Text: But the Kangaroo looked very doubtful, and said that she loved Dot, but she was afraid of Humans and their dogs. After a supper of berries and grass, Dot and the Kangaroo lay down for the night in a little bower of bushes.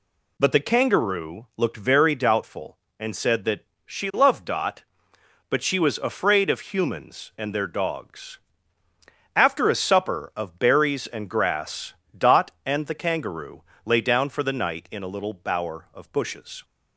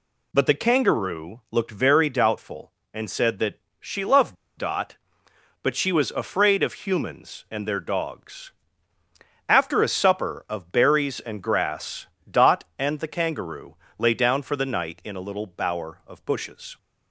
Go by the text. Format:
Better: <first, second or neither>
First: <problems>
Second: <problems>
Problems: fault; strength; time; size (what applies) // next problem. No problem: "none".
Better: first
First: pauses between "that" and "she"; slight; at 3.6 s; 0.20 s long // pauses between "Kangaroo" and "lay"; slight; at 13.6 s; 0.22 s long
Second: pauses between "that" and "she"; slight; at 3.5 s; 0.20 s long // pauses between "loved" and "Dot"; slight; at 4.3 s; 0.23 s long // pauses between "Kangaroo" and "lay"; slight; at 13.7 s; 0.22 s long